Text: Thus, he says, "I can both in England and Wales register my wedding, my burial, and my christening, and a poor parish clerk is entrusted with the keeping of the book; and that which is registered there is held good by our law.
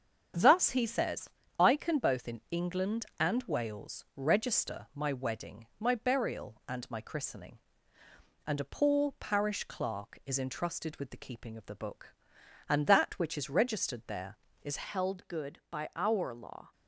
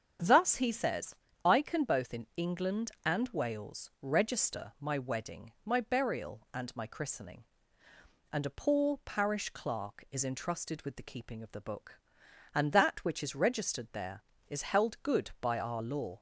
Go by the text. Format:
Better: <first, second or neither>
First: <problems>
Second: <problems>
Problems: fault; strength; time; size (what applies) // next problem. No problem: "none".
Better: second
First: starts louder than the rest; strong; until 1.6 s; 7.5 dB // changes voice at "held"; from 14.8 s on; 1.9 s long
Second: starts louder than the rest; strong; until 1.5 s; 7.5 dB